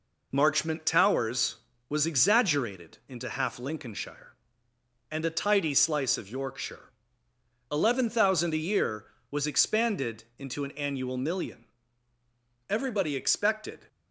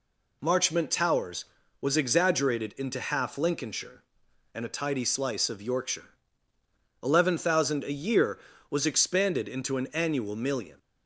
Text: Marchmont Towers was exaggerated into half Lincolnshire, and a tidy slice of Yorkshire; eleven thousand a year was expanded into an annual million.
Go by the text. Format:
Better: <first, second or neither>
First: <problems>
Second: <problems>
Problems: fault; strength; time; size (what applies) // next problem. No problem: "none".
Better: second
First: pauses between "expanded" and "into"; slight; at 10.2 s; 0.16 s long // goes on to say "Everybody expected"; noticeable; from 12.6 s on; 1.1 s long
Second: none